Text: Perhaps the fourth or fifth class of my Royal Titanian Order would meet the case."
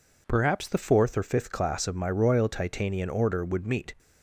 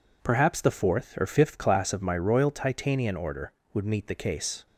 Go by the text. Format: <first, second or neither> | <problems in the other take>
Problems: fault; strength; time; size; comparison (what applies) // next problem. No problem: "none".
second | stops before "the case"; at 3.9 s